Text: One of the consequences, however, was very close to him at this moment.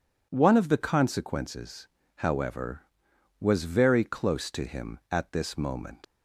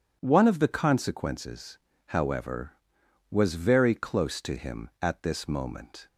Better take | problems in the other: second | leaves "moment" unfinished; at 6.0 s; 115 ms

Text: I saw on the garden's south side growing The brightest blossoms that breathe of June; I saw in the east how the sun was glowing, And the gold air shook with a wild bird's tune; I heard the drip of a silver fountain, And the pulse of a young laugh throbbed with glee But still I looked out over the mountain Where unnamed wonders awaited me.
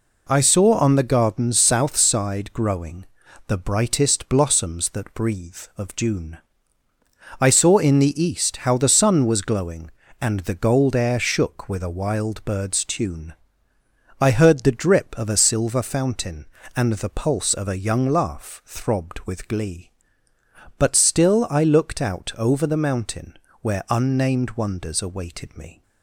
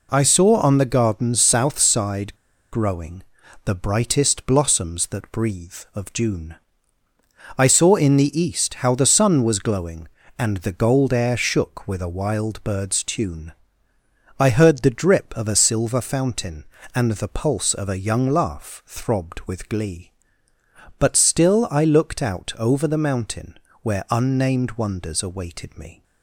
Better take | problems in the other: first | pauses between "side" and "growing"; at 2.3 s; 0.38 s long // pauses between "growing" and "The"; at 3.2 s; 0.42 s long; also in the first // pauses between "mountain" and "Where"; slight; at 23.5 s; 0.24 s long; slight in the first

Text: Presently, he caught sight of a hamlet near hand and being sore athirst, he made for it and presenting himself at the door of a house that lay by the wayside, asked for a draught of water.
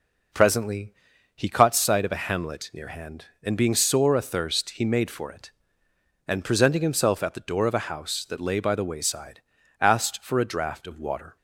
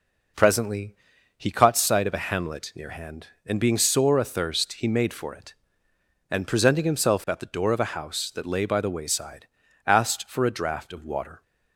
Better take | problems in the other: neither | none

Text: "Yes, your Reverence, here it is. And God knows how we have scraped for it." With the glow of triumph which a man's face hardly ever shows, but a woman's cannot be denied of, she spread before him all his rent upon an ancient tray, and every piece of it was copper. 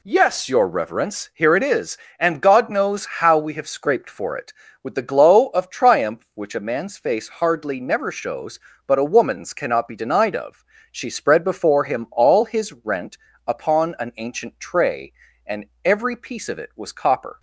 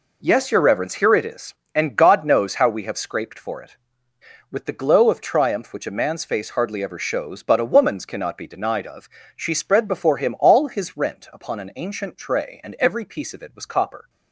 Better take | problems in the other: second | says "never" for "ever"; at 7.7 s // pauses between "rent" and "upon"; slight; at 13.1 s; 0.30 s long // pauses between "and" and "every"; slight; at 15.6 s; 0.18 s long

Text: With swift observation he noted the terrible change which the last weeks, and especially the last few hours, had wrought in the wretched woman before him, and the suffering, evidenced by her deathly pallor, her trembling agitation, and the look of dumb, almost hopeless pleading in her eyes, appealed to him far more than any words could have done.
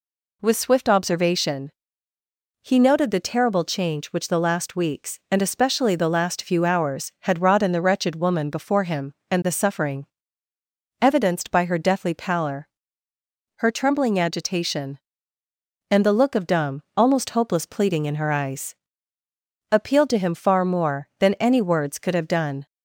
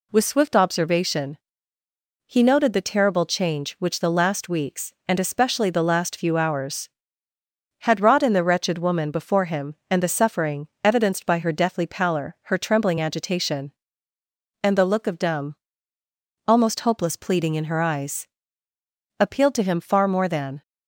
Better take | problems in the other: first | pauses between "observation" and "he"; noticeable; at 1.3 s; 0.94 s long; noticeable in the first // stops before "any words could have done"; at 20.6 s

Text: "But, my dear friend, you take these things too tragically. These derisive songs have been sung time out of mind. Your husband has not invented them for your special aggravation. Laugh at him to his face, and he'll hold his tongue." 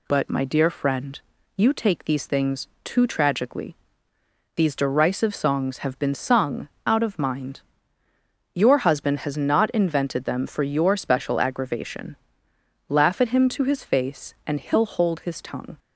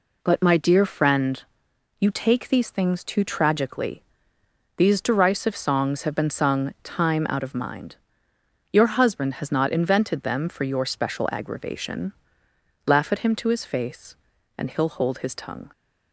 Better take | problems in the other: second | pauses between "things" and "too"; slight; at 2.6 s; 0.16 s long // skips "time"; at 6.7 s

